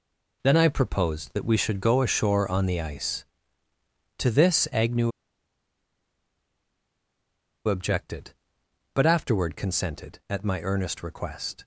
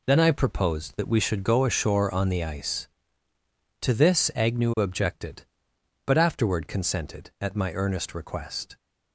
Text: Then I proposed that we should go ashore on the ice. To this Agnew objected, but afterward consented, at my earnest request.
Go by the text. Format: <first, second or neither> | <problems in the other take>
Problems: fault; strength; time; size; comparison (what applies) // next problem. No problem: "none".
second | pauses between "Agnew" and "objected"; strong; at 5.1 s; 2.5 s long